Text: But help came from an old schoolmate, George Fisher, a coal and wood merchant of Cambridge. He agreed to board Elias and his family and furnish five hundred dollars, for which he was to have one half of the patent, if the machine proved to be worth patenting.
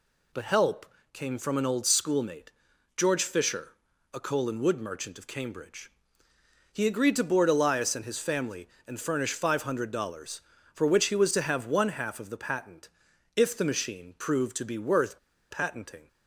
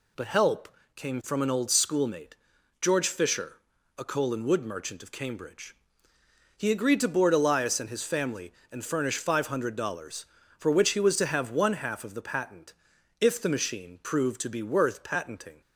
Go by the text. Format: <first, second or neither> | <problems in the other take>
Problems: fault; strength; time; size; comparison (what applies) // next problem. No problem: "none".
second | pauses between "help" and "came"; slight; at 0.8 s; 0.26 s long; slight in the second // pauses between "worth" and "patenting"; slight; at 15.1 s; 0.32 s long